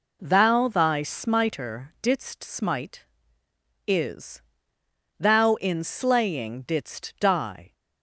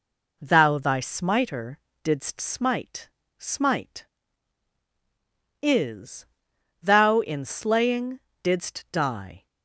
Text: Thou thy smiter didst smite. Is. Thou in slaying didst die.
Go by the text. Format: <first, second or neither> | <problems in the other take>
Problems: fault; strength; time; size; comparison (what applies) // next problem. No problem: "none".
first | pauses between "smiter" and "didst"; slight; at 1.8 s; 0.24 s long // says "smite" twice; at 3.3 s // pauses between "slaying" and "didst"; slight; at 8.2 s; 0.24 s long